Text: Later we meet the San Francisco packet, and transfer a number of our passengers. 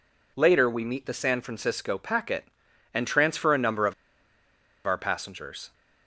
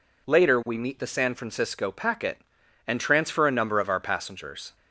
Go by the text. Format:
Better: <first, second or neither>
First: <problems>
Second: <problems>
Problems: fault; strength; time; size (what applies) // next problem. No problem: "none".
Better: second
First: pauses between "of" and "our"; noticeable; at 3.9 s; 0.92 s long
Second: none